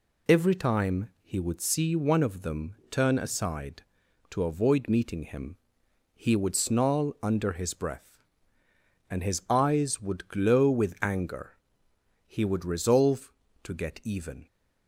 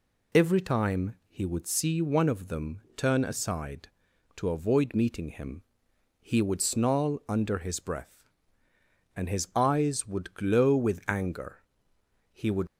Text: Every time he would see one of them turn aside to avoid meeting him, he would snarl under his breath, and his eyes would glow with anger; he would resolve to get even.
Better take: first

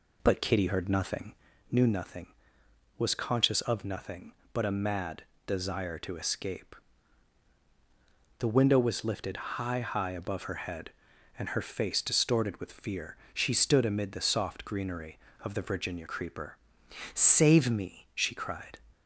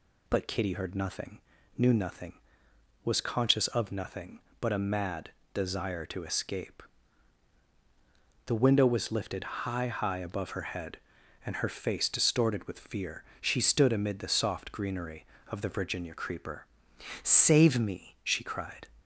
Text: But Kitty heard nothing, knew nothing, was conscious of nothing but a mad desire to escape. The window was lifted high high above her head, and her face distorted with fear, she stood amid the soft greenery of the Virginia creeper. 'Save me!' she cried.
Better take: second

